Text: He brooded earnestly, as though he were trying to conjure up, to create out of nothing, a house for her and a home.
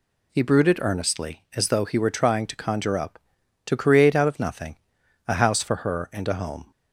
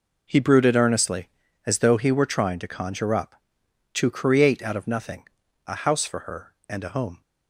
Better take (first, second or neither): neither